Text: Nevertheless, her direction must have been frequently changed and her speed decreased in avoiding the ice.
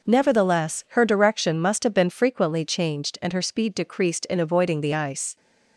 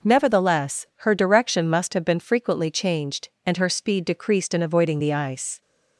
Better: neither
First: none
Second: none

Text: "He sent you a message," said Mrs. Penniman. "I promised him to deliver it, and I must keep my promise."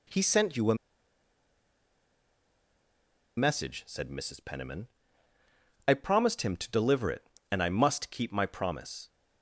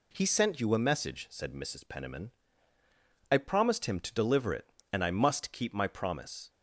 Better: second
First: pauses between "a" and "message"; strong; at 0.7 s; 2.6 s long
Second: none

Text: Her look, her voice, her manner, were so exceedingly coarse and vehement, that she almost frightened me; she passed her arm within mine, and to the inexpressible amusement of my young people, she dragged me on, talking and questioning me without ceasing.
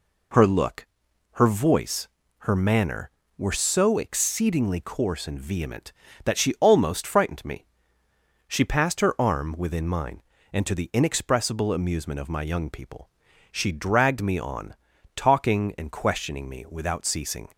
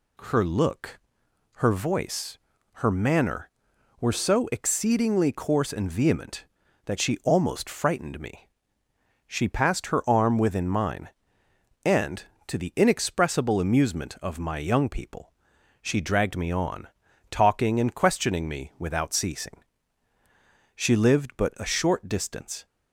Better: first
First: none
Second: goes on to say "She lived but a short distance"; strong; from 20.7 s on; 1.8 s long

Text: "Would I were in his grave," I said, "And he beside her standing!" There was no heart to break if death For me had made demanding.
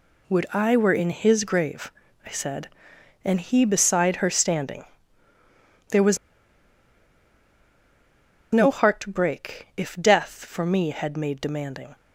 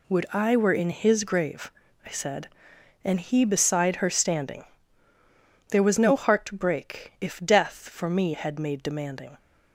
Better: second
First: pauses between "was" and "no"; strong; at 6.1 s; 2.3 s long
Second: none

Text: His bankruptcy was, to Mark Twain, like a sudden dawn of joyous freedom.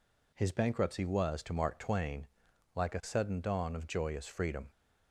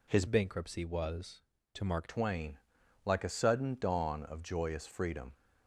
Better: first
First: none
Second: changes voice from "bankruptcy" to "Mark"; from 0.2 to 2.0 s; 1.8 s long

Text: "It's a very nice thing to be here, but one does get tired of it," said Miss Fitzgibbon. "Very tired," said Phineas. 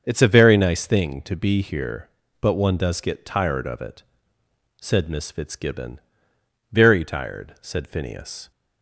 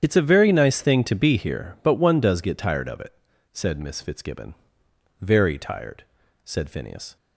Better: first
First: starts louder than the rest; until 1.0 s; 6.5 dB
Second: loses the start of "It's"; at 0.0 s; 40 ms // starts louder than the rest; strong; until 1.0 s; 9 dB

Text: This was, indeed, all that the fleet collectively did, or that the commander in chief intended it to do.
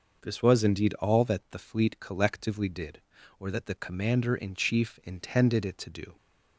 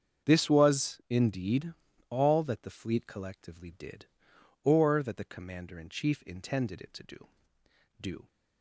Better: first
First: none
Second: starts louder than the rest; strong; until 1.3 s; 7.5 dB // says "do" twice; at 8.0 s

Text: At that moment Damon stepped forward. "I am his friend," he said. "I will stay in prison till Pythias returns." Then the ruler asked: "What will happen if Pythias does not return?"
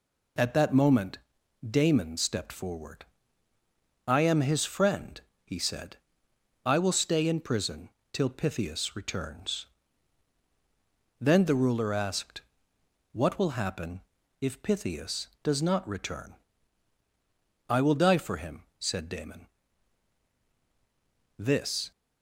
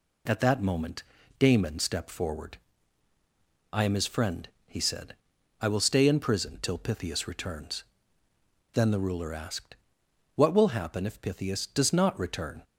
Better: second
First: pauses between "moment" and "Damon"; noticeable; at 1.1 s; 0.50 s long // pauses between "prison" and "till"; slight; at 7.8 s; 0.24 s long // pauses between "happen" and "if"; at 14.0 s; 0.40 s long // goes on to say "I will die for him said Damon This"; strong; from 17.6 s on; 4.2 s long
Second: pauses between "moment" and "Damon"; slight; at 1.0 s; 0.34 s long

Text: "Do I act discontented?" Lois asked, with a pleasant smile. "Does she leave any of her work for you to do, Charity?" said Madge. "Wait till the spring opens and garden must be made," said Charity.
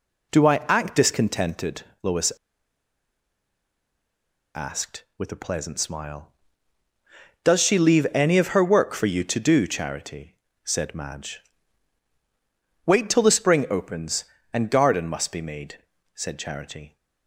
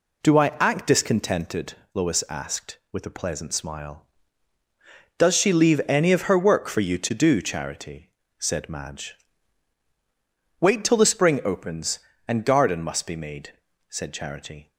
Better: second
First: pauses between "Lois" and "asked"; strong; at 2.3 s; 2.2 s long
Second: none

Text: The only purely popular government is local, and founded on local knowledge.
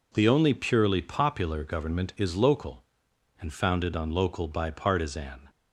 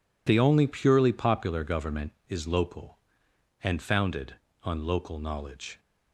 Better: second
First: says "bipartisan" for "knowledge"; at 4.4 s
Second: none

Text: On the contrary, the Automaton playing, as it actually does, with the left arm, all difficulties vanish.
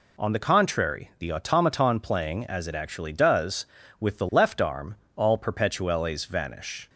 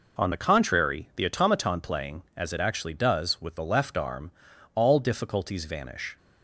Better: second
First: says "perpetuelles" for "difficulties"; at 5.3 s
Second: none

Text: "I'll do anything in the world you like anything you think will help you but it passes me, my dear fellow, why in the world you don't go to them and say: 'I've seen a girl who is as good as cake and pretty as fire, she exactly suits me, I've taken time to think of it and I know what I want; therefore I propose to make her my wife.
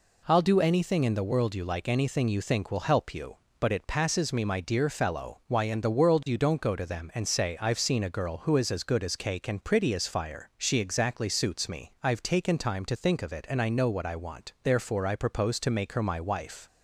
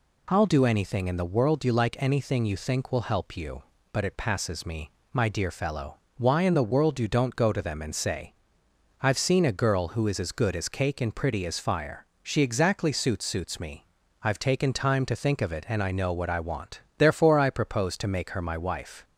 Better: first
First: none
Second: says "suits" twice; at 13.2 s

